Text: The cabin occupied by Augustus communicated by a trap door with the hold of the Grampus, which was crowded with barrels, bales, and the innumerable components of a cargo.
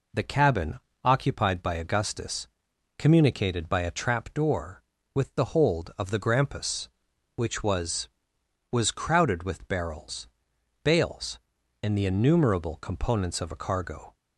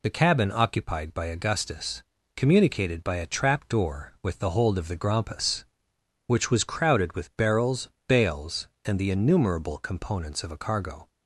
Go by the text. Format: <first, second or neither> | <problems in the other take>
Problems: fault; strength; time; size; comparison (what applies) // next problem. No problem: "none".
second | pauses between "cabin" and "occupied"; slight; at 0.7 s; 0.24 s long // pauses between "Augustus" and "communicated"; noticeable; at 2.4 s; 0.50 s long; slight in the second // says "was" twice; at 8.7 s